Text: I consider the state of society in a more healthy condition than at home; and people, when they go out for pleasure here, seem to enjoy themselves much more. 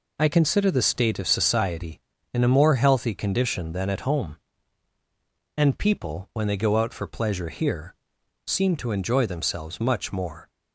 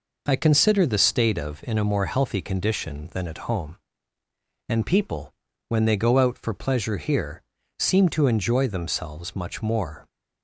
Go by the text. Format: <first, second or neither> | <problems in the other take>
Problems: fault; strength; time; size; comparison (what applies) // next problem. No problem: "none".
first | skips "society"; at 1.6 s